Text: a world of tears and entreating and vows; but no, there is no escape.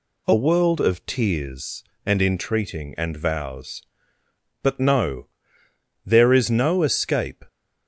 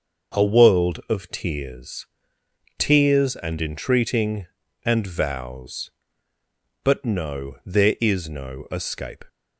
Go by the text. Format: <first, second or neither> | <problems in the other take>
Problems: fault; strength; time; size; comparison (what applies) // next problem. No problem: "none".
first | starts louder than the rest; noticeable; until 1.4 s; 6 dB // says "tears" twice; at 2.7 s